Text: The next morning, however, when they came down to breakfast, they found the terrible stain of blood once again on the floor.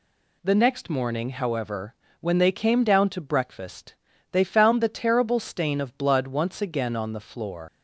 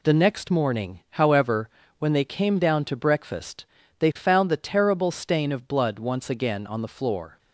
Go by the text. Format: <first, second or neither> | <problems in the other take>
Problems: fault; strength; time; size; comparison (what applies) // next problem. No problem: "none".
second | leaves "floor" unfinished; at 7.6 s; 115 ms